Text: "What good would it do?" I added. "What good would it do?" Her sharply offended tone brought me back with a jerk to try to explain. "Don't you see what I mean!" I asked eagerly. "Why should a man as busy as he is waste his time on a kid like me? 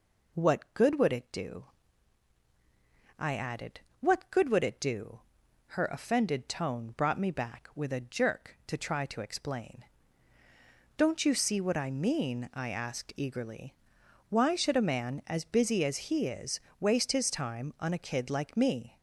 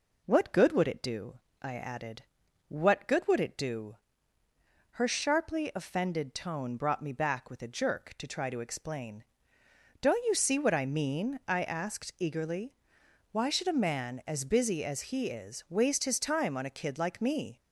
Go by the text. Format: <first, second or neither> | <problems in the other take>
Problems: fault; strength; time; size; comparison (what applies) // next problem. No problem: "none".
second | skips "sharply"; at 5.8 s // pauses between "is" and "waste"; slight; at 16.5 s; 0.22 s long